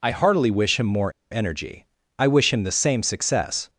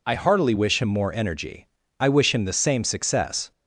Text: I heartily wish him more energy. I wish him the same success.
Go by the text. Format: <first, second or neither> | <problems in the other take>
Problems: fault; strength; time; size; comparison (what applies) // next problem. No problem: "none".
second | pauses between "more" and "energy"; slight; at 1.1 s; 0.21 s long